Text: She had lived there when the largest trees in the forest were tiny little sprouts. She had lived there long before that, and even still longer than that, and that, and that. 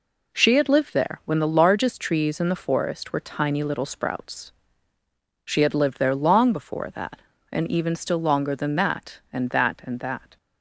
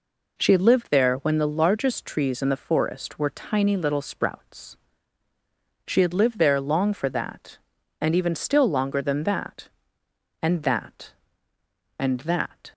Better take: first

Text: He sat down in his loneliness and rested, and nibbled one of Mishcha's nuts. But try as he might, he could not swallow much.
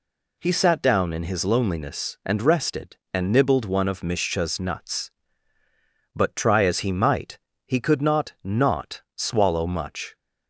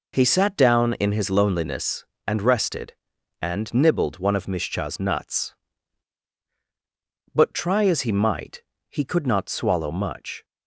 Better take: second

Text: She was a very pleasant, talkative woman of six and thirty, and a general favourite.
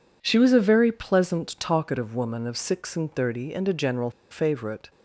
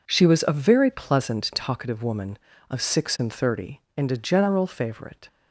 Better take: second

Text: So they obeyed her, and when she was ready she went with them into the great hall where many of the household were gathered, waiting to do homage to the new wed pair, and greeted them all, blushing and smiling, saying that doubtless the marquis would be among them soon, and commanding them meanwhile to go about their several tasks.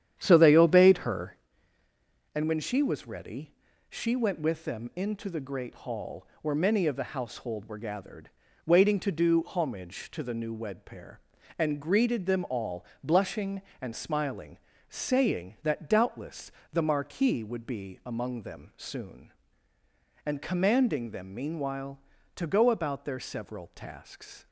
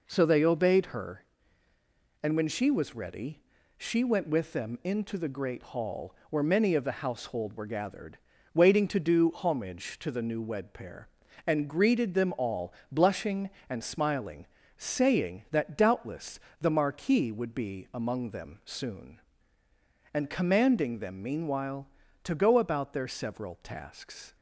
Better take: second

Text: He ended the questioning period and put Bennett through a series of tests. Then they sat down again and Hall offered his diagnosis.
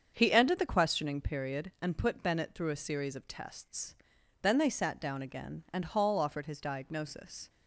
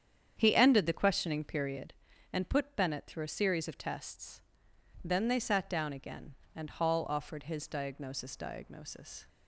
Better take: first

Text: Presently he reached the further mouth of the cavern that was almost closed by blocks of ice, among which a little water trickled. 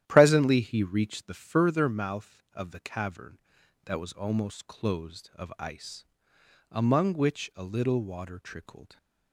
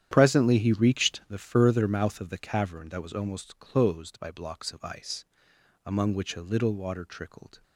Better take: second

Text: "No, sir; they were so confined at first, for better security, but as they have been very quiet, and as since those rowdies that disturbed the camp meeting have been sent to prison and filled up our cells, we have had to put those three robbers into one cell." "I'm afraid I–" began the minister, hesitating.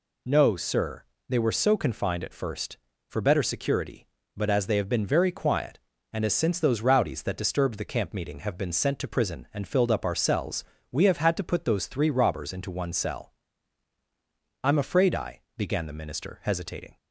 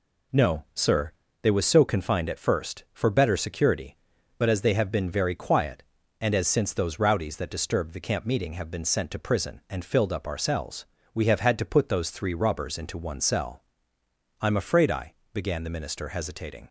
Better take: first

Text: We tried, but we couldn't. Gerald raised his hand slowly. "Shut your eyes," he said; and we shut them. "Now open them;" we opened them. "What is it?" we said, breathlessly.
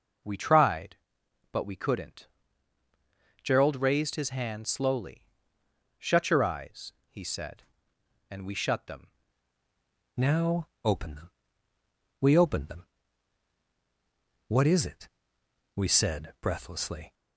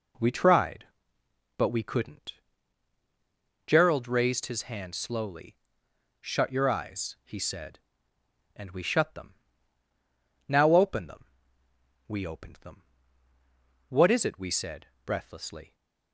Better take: second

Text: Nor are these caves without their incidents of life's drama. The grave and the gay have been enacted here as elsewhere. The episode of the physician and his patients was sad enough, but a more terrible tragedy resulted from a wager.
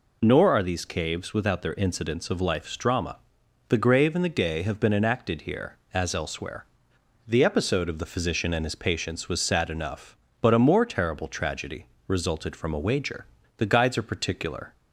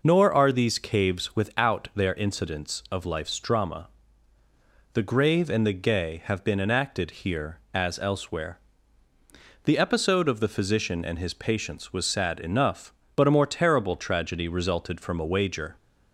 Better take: second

